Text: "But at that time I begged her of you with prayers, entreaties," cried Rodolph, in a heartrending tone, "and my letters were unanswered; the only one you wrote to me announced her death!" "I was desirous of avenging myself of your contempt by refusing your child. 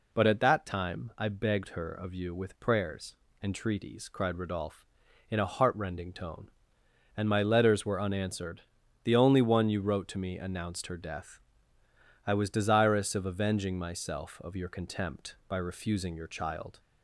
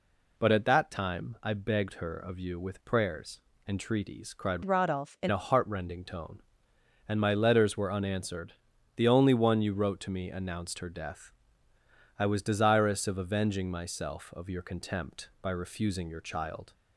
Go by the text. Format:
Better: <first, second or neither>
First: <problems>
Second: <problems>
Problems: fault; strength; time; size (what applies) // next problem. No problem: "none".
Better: first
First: none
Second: changes voice from "Rodolph" to "in"; from 4.6 to 5.2 s; 0.6 s long